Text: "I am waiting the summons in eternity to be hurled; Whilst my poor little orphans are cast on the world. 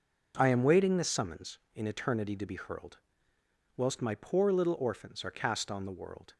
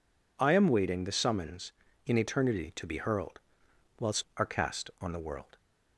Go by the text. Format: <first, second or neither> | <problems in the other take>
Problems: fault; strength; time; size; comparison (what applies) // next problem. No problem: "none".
first | skips "my poor little orphans"; at 4.3 s